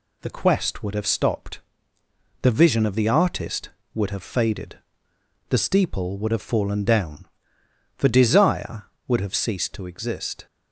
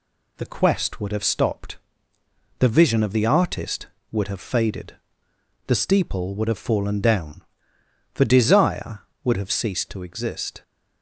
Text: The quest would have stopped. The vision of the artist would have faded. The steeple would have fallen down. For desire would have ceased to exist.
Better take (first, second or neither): neither